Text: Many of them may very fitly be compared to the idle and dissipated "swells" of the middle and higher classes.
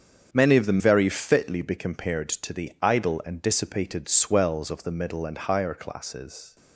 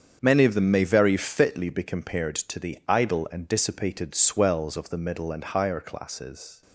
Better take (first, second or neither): second